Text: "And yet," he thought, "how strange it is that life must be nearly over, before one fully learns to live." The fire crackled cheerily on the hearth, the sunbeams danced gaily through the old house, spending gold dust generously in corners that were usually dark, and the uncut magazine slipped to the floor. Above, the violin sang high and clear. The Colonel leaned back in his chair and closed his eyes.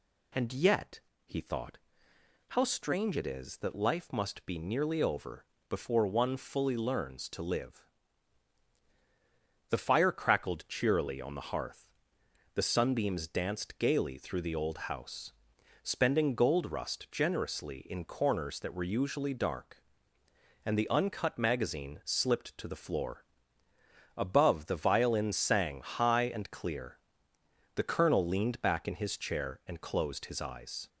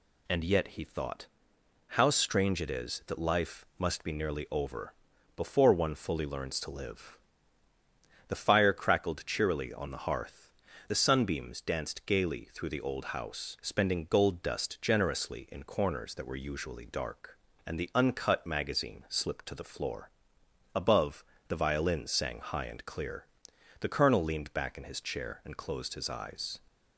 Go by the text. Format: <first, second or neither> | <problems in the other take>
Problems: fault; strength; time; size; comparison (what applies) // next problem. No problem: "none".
second | says "rust" for "dust"; at 16.7 s